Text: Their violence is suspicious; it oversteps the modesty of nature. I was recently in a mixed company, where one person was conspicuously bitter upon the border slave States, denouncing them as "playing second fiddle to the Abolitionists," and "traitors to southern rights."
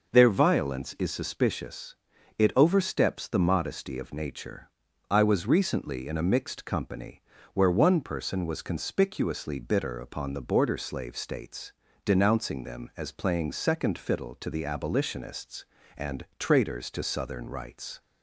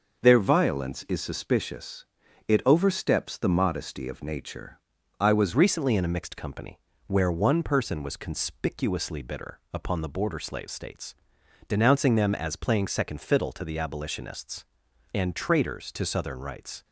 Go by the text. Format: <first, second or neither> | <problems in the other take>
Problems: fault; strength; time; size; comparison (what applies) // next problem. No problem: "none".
first | starts louder than the rest; noticeable; until 1.2 s; 6 dB // changes voice at "recently"; from 5.5 s on; 11.3 s long